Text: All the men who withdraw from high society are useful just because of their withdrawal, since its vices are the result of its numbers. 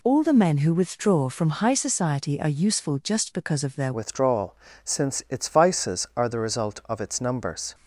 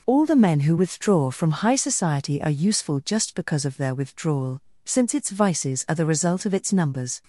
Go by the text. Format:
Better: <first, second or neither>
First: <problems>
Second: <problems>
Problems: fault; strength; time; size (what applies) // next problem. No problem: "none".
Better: second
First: changes voice at "withdrawal"; from 3.9 s on; 3.8 s long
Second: none